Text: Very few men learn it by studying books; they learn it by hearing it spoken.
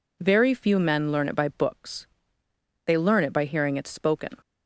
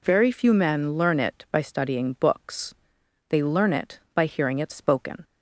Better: second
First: skips "studying"; at 1.4 s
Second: none

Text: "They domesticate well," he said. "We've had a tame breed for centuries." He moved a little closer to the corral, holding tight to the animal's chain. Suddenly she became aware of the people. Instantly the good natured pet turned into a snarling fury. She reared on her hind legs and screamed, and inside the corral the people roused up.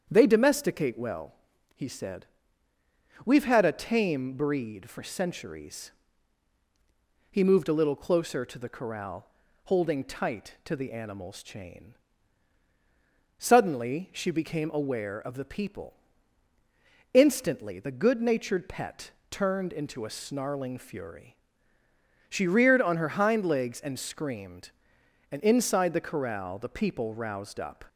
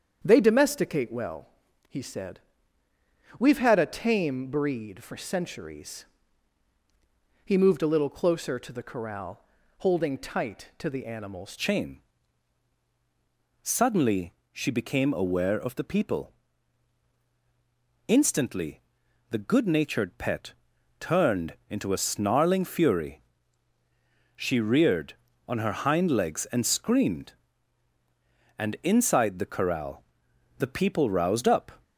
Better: first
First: starts louder than the rest; strong; until 1.1 s; 7.5 dB // pauses between "pet" and "turned"; slight; at 19.1 s; 0.17 s long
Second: starts louder than the rest; strong; until 1.2 s; 7.5 dB // changes voice at "chain"; from 11.5 s on; 20.3 s long // pauses between "Suddenly" and "she"; slight; at 14.3 s; 0.18 s long // pauses between "Instantly" and "the"; noticeable; at 18.8 s; 0.48 s long // pauses between "pet" and "turned"; noticeable; at 20.5 s; 0.46 s long // pauses between "corral" and "the"; noticeable; at 30.0 s; 0.54 s long

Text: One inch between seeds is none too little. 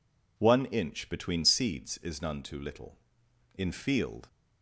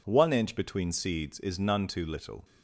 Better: second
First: goes on to say "In field"; noticeable; from 3.5 s on; 0.72 s long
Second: none

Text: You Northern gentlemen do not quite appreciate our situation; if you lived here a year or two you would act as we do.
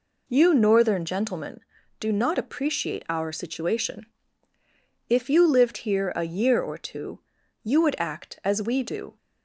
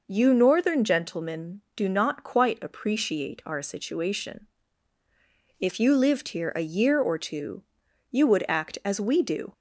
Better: second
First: skips "quite"; at 2.3 s // pauses between "two" and "you"; at 7.2 s; 0.42 s long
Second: pauses between "two" and "you"; noticeable; at 7.6 s; 0.48 s long

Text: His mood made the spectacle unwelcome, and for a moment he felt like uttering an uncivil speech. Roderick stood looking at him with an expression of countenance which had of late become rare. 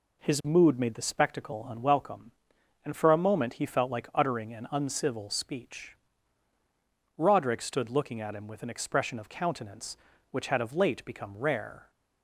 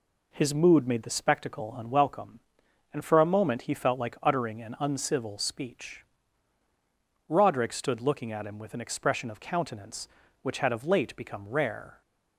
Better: neither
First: none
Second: none

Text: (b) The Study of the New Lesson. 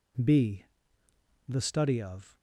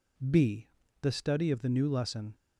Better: second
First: stops before "the New Lesson"; at 2.3 s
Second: none

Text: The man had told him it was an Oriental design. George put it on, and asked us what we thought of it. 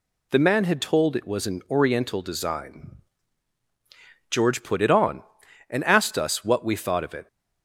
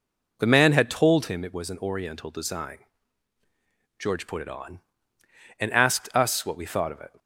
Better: second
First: skips "him"; at 1.1 s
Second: none

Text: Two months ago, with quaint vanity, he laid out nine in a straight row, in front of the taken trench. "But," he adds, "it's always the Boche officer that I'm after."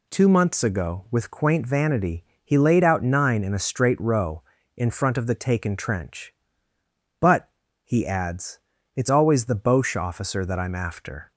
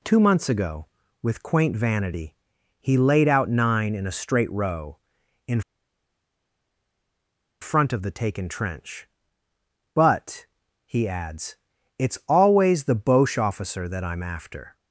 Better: first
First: none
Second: pauses between "in" and "front"; strong; at 5.6 s; 2.0 s long

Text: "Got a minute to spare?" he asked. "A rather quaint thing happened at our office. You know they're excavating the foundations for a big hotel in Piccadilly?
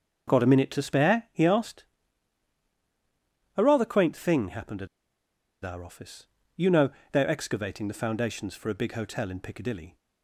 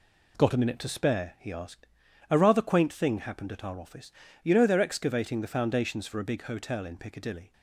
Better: second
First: starts louder than the rest; until 1.4 s; 6.5 dB // pauses between "at" and "our"; noticeable; at 4.8 s; 0.77 s long // pauses between "know" and "they're"; slight; at 6.9 s; 0.20 s long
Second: none

